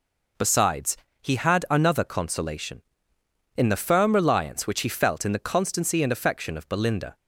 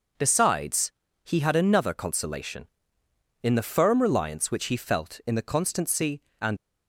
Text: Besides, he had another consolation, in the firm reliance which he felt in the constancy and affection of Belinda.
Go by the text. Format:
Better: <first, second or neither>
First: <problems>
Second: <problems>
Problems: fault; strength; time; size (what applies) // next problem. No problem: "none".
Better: first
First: none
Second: stops before "affection of Belinda"; at 6.5 s